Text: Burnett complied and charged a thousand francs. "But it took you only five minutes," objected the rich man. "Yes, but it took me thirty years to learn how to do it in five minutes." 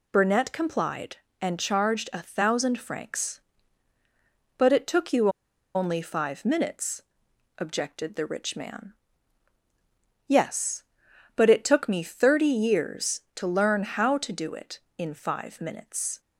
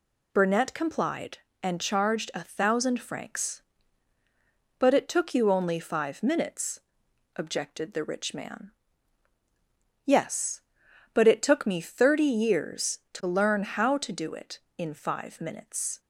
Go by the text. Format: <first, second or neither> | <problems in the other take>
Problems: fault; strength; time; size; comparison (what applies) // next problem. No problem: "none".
second | pauses between "you" and "only"; noticeable; at 5.2 s; 0.46 s long